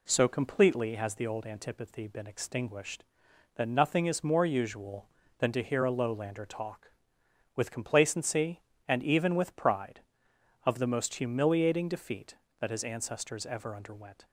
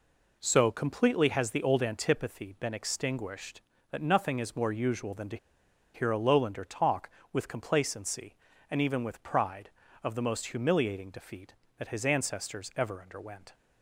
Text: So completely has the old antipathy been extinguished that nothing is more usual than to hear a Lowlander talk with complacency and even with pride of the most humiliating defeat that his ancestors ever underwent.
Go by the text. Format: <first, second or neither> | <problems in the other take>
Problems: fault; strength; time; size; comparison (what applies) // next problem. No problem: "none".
first | pauses between "to" and "hear"; noticeable; at 5.3 s; 0.57 s long